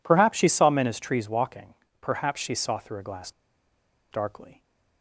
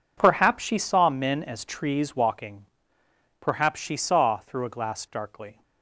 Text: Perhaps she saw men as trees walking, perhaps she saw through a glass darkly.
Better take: second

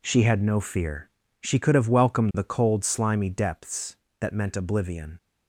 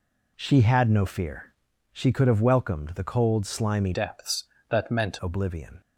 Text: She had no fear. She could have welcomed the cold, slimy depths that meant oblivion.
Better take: first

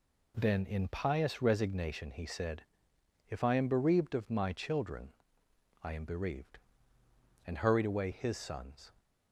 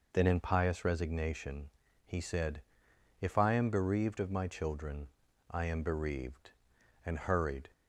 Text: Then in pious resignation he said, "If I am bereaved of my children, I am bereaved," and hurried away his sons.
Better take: first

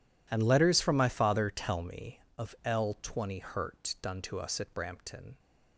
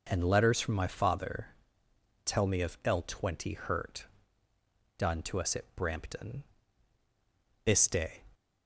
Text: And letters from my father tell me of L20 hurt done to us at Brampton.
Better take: first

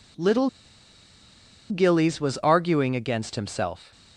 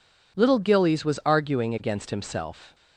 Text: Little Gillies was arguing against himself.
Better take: second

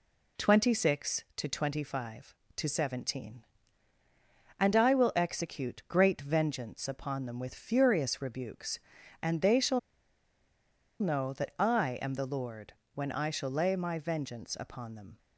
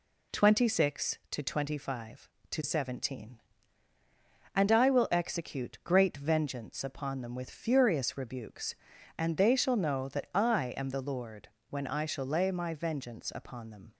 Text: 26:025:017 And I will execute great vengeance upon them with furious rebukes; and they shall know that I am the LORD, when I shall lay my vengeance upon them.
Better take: second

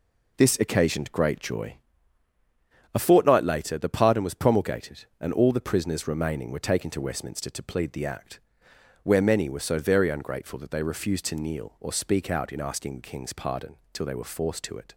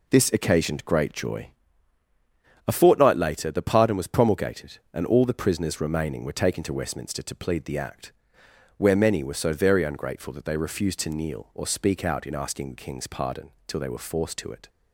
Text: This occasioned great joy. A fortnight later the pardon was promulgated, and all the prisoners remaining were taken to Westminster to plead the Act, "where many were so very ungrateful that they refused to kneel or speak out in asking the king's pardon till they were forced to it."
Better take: neither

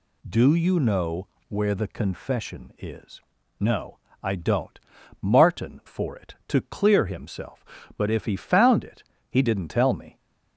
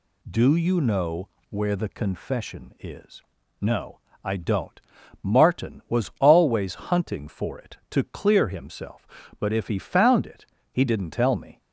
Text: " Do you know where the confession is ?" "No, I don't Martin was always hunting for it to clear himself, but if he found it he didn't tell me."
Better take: second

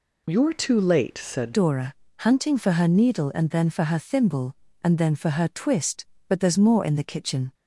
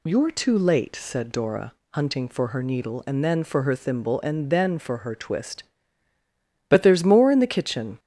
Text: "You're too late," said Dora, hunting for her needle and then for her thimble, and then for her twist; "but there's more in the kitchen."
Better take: second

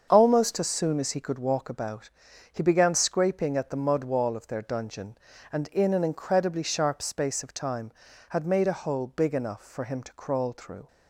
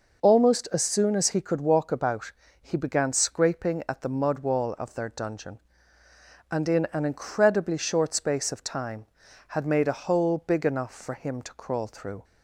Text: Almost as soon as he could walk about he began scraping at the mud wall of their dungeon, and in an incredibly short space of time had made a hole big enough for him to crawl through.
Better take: second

